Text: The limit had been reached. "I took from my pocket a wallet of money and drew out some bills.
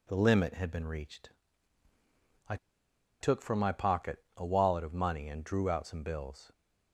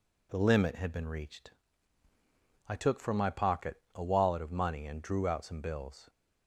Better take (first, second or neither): second